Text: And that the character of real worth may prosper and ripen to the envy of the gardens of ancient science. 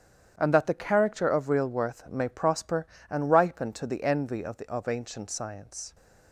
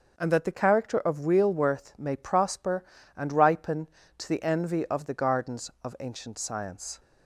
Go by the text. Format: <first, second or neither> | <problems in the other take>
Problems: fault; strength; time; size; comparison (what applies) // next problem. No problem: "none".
second | starts louder than the rest; strong; until 1.3 s; 9.5 dB; also in the second // skips "gardens"; at 4.6 s